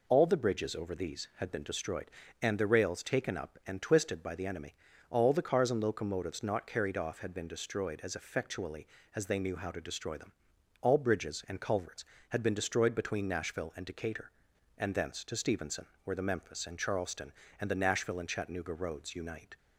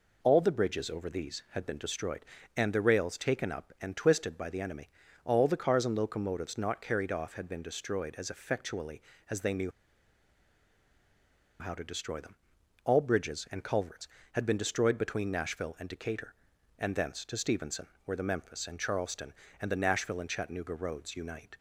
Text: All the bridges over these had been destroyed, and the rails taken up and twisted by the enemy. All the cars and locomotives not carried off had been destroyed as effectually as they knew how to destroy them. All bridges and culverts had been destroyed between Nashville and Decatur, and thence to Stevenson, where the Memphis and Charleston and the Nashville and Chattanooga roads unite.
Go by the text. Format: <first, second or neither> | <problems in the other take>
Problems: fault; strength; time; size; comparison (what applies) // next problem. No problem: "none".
first | pauses between "knew" and "how"; strong; at 9.7 s; 1.8 s long